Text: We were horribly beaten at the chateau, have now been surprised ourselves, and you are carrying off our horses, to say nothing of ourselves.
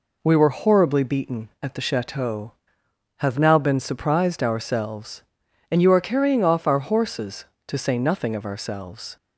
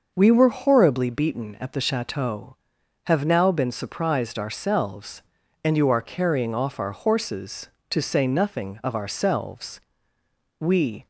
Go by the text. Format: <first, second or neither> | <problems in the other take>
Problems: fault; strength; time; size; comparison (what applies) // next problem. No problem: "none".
first | starts louder than the rest; noticeable; until 1.1 s; 6 dB // goes on to say "We"; slight; from 10.5 s on; 0.48 s long